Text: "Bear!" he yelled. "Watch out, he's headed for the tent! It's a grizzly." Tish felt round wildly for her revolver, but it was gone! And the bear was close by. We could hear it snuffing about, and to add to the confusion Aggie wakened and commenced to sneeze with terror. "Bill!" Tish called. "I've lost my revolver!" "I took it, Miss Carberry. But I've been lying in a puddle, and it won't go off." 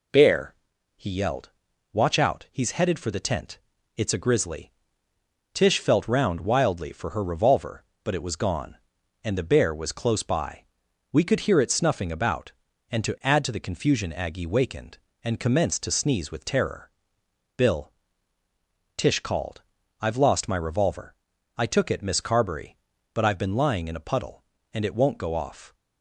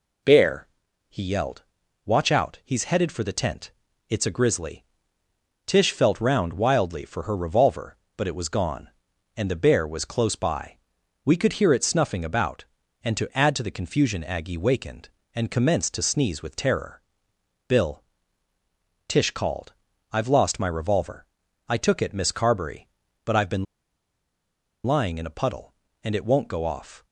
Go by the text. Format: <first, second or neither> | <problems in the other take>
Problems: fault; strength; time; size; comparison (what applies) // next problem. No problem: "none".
first | pauses between "been" and "lying"; at 23.6 s; 1.1 s long